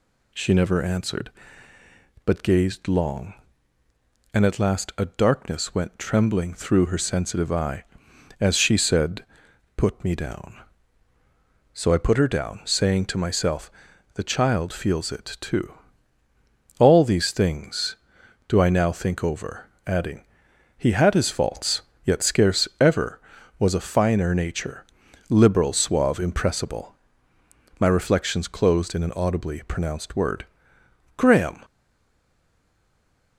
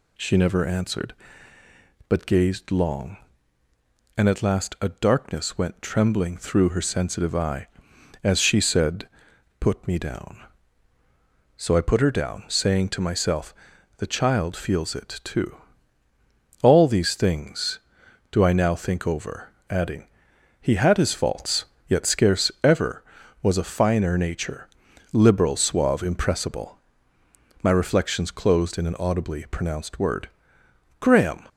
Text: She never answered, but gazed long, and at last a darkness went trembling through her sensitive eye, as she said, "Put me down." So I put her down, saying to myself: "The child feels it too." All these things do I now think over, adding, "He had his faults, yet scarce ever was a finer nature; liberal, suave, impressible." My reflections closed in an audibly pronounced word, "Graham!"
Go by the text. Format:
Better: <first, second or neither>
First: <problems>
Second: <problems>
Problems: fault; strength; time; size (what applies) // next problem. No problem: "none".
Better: second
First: stays silent after the last word; noticeable; from 31.6 s on; 1.7 s long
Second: none